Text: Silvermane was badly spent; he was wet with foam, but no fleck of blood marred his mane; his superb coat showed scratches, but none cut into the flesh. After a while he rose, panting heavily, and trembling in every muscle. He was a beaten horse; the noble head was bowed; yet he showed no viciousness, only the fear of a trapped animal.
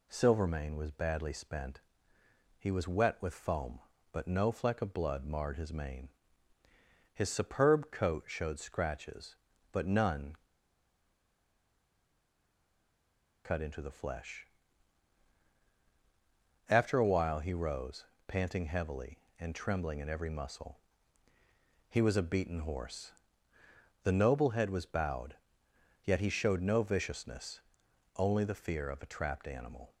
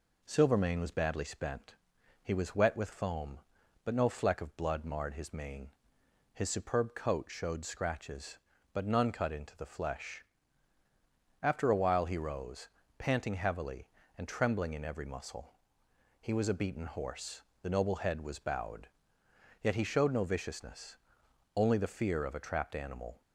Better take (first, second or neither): second